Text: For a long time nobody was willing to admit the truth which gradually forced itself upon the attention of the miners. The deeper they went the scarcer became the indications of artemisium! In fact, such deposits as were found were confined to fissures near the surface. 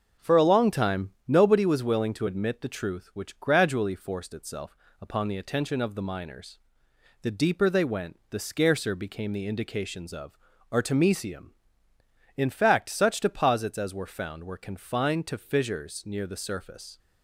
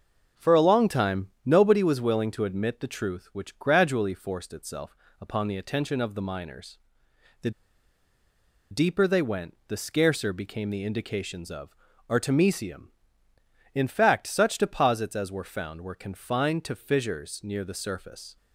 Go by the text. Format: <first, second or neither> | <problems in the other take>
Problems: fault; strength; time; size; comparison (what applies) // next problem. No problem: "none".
first | starts louder than the rest; noticeable; until 1.5 s; 6 dB; noticeable in the first // pauses between "itself" and "upon"; slight; at 4.9 s; 0.24 s long; slight in the first // pauses between "The" and "deeper"; at 7.4 s; 1.2 s long // pauses between "of" and "artemisium"; at 11.6 s; 0.40 s long; also in the first